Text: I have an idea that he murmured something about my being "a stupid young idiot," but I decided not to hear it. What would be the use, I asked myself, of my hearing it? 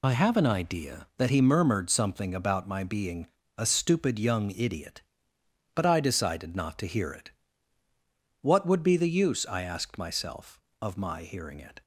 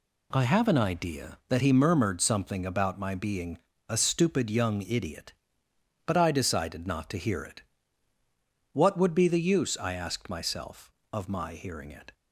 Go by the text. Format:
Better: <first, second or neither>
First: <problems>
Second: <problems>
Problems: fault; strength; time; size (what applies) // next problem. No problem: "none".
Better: second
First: loses the start of "I"; at 0.0 s; 45 ms // pauses between "being" and "a"; slight; at 3.2 s; 0.32 s long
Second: pauses between "being" and "a"; slight; at 3.5 s; 0.32 s long